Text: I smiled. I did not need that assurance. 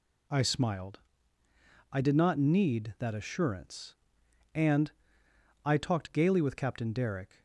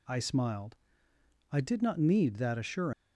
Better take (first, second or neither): second